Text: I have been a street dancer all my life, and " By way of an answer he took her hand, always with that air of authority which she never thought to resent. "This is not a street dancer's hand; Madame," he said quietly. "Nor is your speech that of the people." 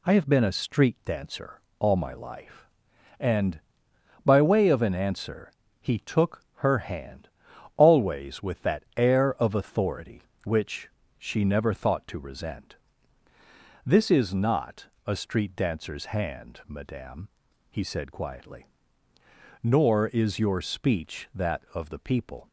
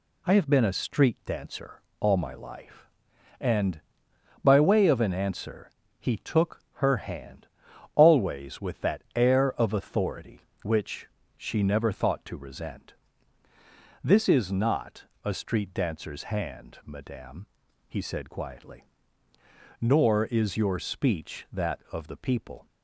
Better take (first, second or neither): neither